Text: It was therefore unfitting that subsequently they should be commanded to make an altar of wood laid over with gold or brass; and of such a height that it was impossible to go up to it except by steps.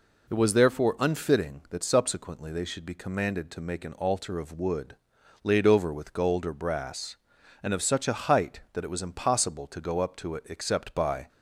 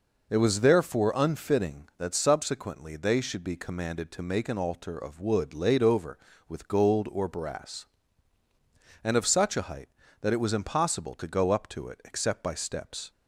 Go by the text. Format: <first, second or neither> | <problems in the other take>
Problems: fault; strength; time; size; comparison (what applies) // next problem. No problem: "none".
second | pauses between "wood" and "laid"; noticeable; at 4.9 s; 0.46 s long // stops before "steps"; at 11.2 s